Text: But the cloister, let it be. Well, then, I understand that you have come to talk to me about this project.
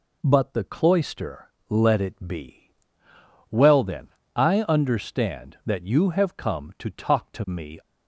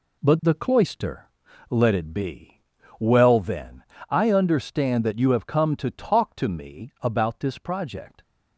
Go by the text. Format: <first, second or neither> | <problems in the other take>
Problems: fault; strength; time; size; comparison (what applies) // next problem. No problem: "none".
second | stops before "about this project"; at 7.7 s